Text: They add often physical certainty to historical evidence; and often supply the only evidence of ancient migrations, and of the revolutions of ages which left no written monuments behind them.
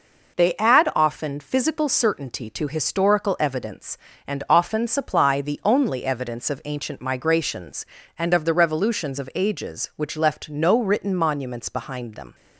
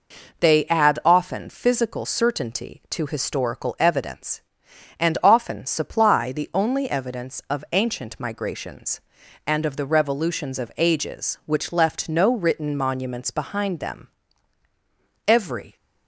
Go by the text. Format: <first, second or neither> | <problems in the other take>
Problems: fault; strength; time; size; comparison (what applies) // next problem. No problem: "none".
first | goes on to say "Every"; slight; from 15.2 s on; 0.48 s long